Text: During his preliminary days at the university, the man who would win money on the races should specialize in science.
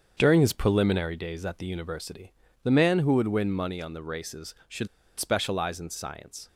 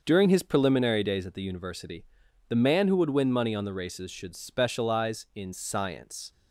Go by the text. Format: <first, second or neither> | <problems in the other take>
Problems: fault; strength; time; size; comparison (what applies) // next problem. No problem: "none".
second | starts louder than the rest; until 1.1 s; 7 dB; also in the second // pauses between "should" and "specialize"; slight; at 4.8 s; 0.31 s long